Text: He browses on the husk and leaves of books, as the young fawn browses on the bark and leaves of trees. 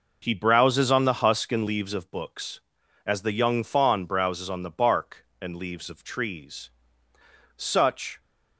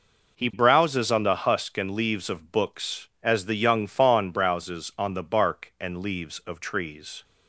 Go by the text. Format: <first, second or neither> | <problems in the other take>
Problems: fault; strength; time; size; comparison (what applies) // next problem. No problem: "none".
second | goes on to say "Such"; noticeable; from 7.5 s on; 0.64 s long